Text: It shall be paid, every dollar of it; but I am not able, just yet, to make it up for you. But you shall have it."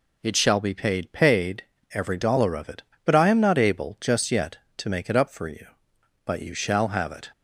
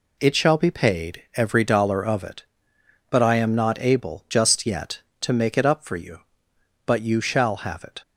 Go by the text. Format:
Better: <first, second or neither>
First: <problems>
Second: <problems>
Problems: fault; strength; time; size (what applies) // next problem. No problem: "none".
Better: second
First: says "paid" twice; at 1.1 s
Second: none